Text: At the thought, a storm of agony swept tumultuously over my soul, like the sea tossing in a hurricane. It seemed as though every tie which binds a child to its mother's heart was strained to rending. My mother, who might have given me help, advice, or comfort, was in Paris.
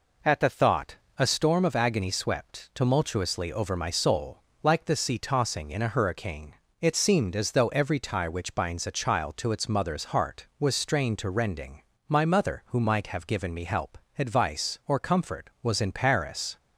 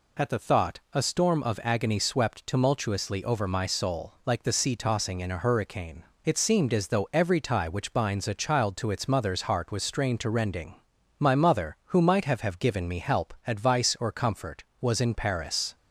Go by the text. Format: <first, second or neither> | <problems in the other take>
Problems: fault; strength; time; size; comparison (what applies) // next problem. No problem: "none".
first | says "have" twice; at 12.3 s